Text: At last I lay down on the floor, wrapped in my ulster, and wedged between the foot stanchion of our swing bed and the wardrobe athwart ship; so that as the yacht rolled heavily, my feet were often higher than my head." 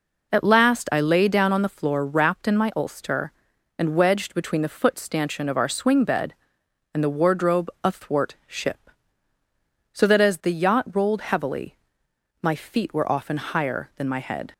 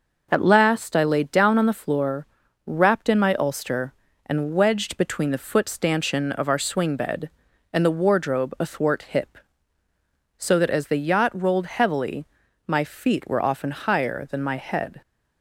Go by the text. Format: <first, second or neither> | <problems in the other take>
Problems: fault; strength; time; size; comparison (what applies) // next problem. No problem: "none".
first | says "hip" for "ship"; at 9.0 s